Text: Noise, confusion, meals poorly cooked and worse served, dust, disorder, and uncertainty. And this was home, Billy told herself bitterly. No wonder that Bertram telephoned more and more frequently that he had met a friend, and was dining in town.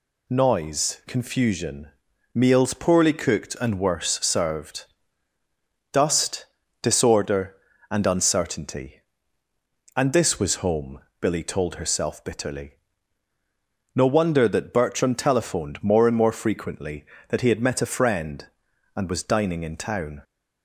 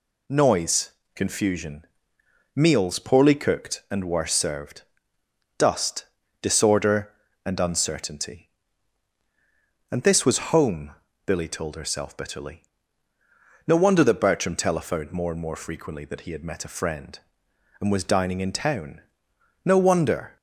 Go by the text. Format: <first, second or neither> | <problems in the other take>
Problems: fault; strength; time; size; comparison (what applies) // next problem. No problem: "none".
first | goes on to say "No wonder"; noticeable; from 19.6 s on; 0.74 s long